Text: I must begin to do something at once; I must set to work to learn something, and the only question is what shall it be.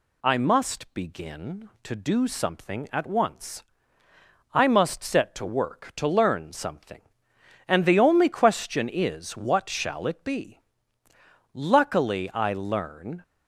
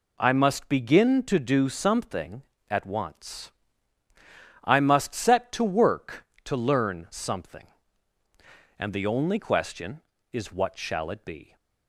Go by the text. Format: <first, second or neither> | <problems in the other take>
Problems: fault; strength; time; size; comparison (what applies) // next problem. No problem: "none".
second | goes on to say "Luckily I learn"; strong; from 11.5 s on; 1.6 s long